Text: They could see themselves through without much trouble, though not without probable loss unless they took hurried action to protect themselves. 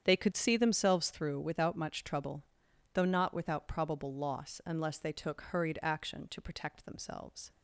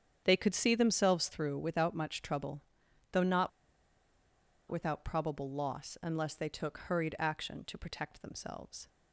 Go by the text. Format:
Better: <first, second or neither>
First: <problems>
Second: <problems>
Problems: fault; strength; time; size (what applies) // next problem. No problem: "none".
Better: first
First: starts louder than the rest; strong; until 1.0 s; 8.5 dB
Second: starts louder than the rest; strong; until 1.2 s; 8.5 dB // pauses between "not" and "without"; at 3.4 s; 1.1 s long